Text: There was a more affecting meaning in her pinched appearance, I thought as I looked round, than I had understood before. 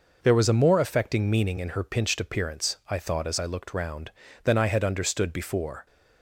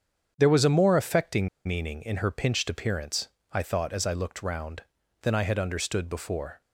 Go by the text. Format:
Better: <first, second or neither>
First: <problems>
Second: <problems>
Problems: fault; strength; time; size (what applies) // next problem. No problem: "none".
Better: first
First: none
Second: starts louder than the rest; strong; until 1.3 s; 8 dB // pauses between "affecting" and "meaning"; slight; at 1.4 s; 0.17 s long